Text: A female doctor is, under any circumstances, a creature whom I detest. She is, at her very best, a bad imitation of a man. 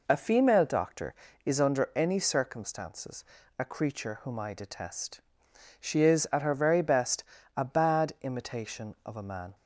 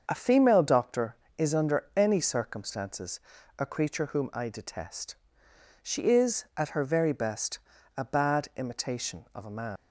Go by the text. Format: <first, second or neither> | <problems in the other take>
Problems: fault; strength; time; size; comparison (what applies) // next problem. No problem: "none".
first | starts louder than the rest; until 1.0 s; 6.5 dB // leaves "man" unfinished; at 9.7 s; 85 ms